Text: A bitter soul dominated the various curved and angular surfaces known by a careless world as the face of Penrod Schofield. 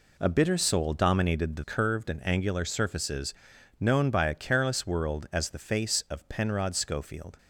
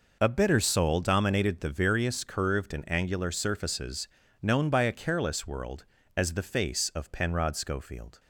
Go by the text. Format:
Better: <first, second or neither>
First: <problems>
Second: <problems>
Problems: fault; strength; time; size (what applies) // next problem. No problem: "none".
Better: second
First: skips "various"; at 1.6 s // pauses between "surfaces" and "known"; noticeable; at 3.3 s; 0.48 s long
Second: pauses between "surfaces" and "known"; slight; at 4.0 s; 0.34 s long